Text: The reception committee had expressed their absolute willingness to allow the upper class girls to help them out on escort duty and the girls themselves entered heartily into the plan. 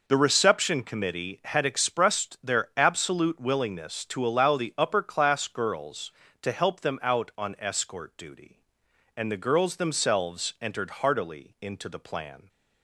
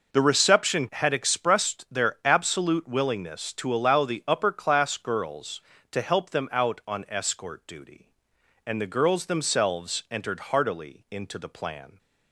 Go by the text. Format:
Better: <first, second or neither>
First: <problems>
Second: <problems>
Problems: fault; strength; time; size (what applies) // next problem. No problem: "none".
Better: first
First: none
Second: skips "committee"; at 0.8 s